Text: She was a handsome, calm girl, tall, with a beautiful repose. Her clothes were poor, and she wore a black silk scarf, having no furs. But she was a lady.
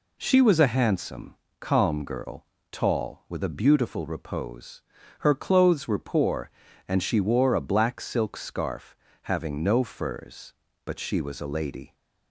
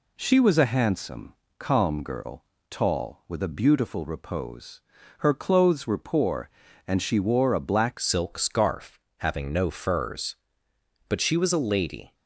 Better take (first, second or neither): first